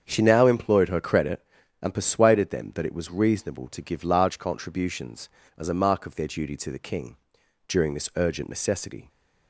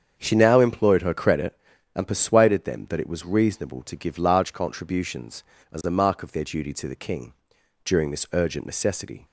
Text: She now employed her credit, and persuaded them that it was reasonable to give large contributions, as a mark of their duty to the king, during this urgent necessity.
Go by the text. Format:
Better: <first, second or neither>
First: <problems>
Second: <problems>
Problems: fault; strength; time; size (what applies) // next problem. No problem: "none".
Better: neither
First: starts louder than the rest; strong; until 1.0 s; 7.5 dB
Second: starts louder than the rest; strong; until 1.1 s; 7.5 dB